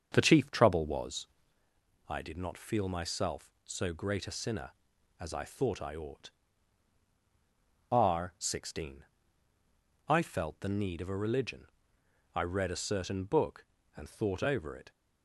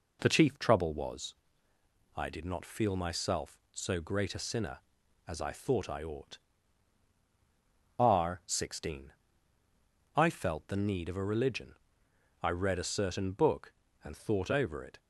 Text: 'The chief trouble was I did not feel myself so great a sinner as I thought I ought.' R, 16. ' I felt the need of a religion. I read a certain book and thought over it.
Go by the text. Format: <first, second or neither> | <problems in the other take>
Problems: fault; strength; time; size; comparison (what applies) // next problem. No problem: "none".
second | starts louder than the rest; strong; until 1.6 s; 7 dB // pauses between "was" and "I"; noticeable; at 1.2 s; 0.80 s long; noticeable in the second